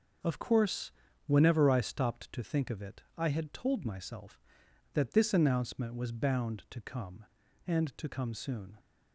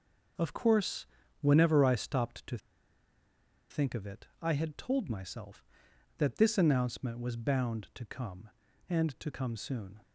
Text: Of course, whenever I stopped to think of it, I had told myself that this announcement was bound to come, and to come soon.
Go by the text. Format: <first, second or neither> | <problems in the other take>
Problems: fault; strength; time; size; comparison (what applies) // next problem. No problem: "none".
first | starts louder than the rest; noticeable; until 1.7 s; 6 dB; noticeable in the first // pauses between "to" and "think"; at 2.5 s; 1.1 s long